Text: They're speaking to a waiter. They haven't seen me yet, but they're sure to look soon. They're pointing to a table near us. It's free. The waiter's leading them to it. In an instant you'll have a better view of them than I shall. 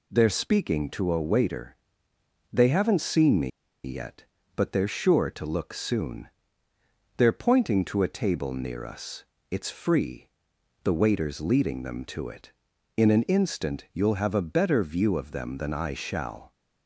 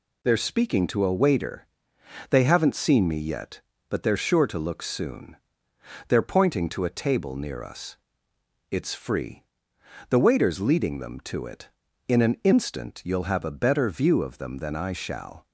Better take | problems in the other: second | pauses between "me" and "yet"; slight; at 3.4 s; 0.35 s long

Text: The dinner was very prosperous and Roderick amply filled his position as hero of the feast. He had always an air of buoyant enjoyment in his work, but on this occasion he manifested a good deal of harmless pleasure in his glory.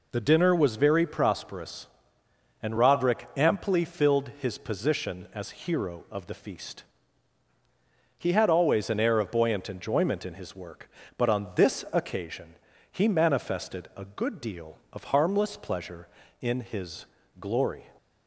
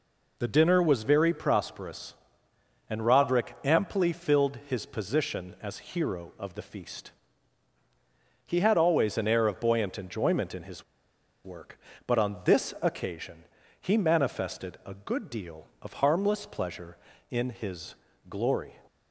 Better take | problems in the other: first | pauses between "his" and "work"; noticeable; at 10.8 s; 0.60 s long // pauses between "occasion" and "he"; slight; at 13.4 s; 0.36 s long; slight in the first // pauses between "his" and "glory"; slight; at 17.9 s; 0.34 s long; slight in the first

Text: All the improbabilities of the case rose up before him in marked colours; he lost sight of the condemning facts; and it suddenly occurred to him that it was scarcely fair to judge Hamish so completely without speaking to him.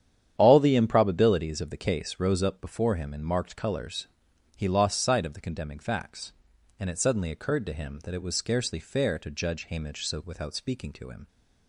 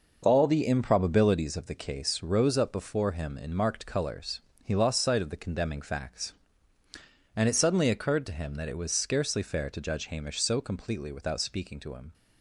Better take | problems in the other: second | starts louder than the rest; strong; until 1.3 s; 9.5 dB // skips "completely"; at 10.2 s

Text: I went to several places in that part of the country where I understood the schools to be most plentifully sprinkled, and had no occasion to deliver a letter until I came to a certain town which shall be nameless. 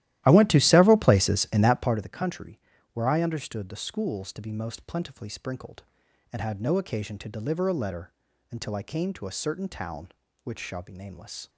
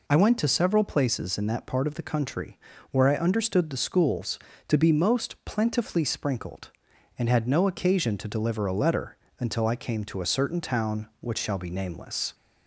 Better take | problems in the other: second | starts louder than the rest; strong; until 2.1 s; 14.5 dB // pauses between "country" and "where"; slight; at 2.5 s; 0.34 s long; slight in the second // pauses between "letter" and "until"; at 8.1 s; 0.40 s long; slight in the second

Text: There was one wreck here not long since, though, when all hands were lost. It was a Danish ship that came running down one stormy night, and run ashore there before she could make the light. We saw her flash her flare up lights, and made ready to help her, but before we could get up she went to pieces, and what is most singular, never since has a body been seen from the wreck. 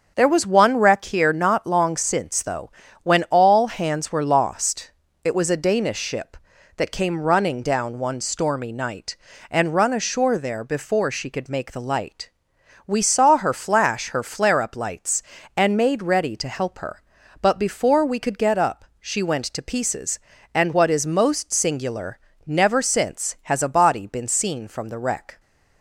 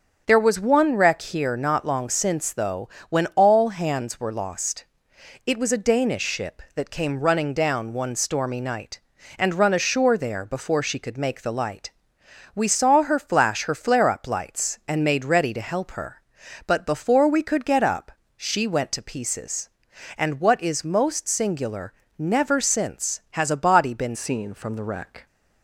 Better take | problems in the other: first | starts louder than the rest; until 1.2 s; 6.5 dB; also in the first // pauses between "up" and "she"; slight; at 18.1 s; 0.26 s long; slight in the first // changes voice at "seen"; from 24.1 s on; 1.1 s long

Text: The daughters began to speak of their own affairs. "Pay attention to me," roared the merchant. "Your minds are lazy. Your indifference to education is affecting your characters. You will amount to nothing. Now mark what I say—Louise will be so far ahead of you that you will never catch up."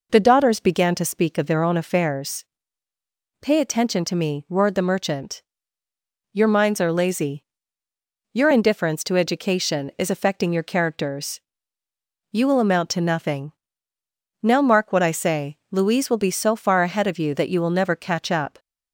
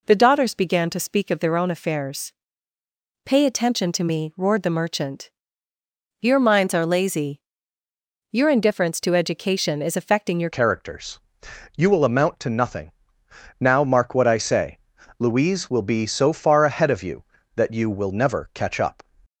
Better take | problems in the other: first | changes voice at "characters"; from 10.5 s on; 8.5 s long

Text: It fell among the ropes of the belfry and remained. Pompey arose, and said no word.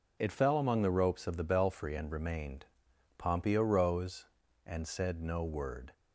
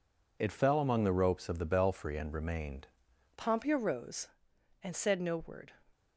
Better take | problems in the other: first | changes voice at "Pompey"; from 3.3 s on; 2.4 s long

